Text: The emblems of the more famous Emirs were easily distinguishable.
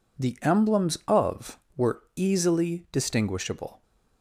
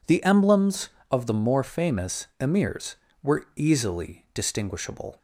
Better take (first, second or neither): second